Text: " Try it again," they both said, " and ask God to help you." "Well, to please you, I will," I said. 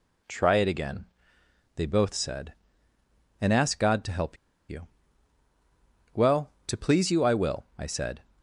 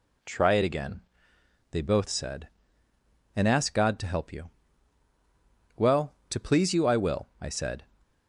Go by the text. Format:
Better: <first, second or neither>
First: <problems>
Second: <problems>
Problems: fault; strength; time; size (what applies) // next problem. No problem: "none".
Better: second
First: pauses between "help" and "you"; slight; at 4.3 s; 0.34 s long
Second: none